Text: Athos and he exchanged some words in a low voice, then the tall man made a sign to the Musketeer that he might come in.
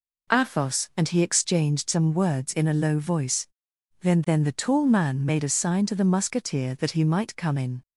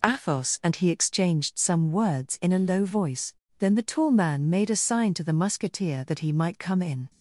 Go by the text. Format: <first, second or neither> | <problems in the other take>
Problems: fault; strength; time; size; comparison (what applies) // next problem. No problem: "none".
second | says "then" twice; at 4.2 s